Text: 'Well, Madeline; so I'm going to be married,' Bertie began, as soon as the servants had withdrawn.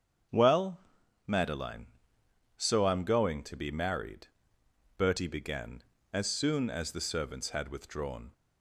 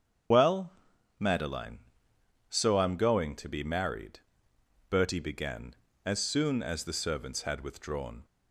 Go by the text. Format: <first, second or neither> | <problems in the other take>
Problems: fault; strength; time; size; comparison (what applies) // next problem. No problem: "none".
first | loses the start of "Well"; at 0.3 s; 70 ms // starts louder than the rest; strong; until 1.7 s; 8 dB; strong in the first